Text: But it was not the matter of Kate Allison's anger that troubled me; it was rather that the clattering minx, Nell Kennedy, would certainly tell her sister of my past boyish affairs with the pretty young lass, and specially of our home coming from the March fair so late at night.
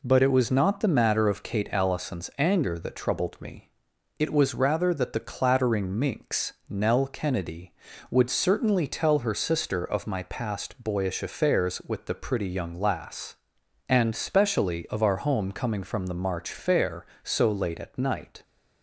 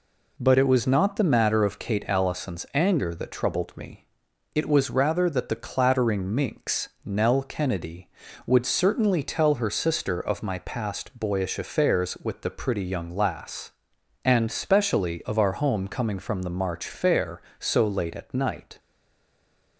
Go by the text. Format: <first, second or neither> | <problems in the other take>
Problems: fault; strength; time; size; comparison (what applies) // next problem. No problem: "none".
first | stays silent after the last word; from 18.7 s on; 1.0 s long